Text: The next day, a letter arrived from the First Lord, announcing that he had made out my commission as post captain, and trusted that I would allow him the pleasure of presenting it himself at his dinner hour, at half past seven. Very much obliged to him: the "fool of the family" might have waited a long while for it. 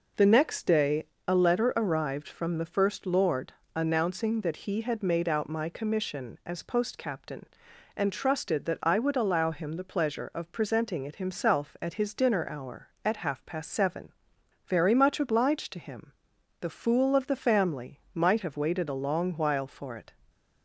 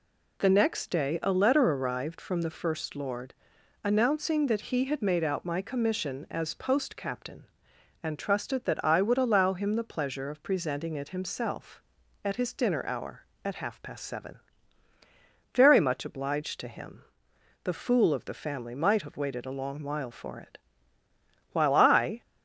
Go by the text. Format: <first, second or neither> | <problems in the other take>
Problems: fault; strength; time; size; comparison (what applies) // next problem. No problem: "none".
first | goes on to say "While I"; noticeable; from 21.5 s on; 0.68 s long